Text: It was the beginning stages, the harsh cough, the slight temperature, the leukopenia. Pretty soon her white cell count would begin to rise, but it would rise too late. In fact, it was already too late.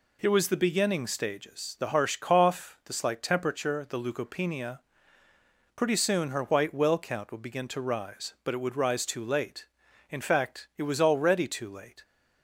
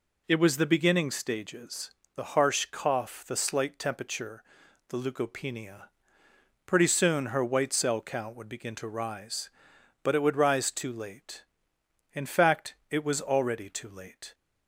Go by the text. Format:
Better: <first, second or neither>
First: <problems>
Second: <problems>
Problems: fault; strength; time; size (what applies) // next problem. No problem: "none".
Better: second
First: says "well" for "cell"; at 6.7 s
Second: none